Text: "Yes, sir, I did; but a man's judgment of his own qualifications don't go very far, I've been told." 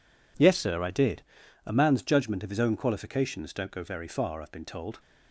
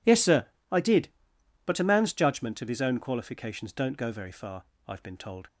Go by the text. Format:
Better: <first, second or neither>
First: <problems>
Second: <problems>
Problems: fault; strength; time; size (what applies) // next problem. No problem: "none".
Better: second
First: skips "but"; at 1.4 s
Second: none